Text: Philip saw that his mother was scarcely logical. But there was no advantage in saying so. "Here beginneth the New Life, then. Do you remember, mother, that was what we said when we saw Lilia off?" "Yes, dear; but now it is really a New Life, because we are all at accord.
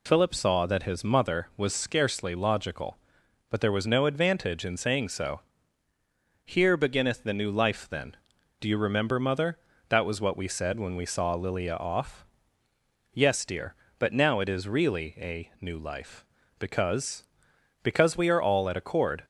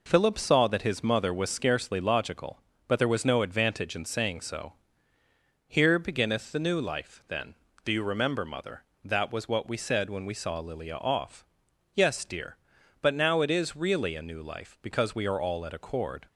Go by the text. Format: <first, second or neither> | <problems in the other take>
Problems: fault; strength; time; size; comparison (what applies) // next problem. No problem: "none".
second | says "because" twice; at 17.8 s